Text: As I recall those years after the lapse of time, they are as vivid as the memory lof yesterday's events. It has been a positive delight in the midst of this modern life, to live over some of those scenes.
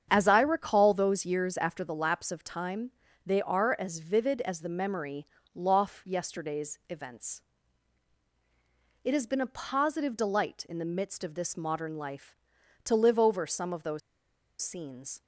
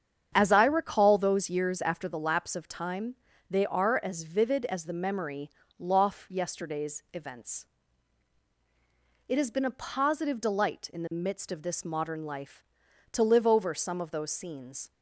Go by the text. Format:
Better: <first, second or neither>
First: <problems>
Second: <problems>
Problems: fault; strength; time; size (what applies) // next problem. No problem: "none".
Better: second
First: starts louder than the rest; strong; until 1.1 s; 8 dB // pauses between "memory" and "lof"; slight; at 5.2 s; 0.28 s long // pauses between "those" and "scenes"; noticeable; at 14.0 s; 0.62 s long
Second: starts louder than the rest; strong; until 1.3 s; 8 dB // pauses between "memory" and "lof"; slight; at 5.4 s; 0.28 s long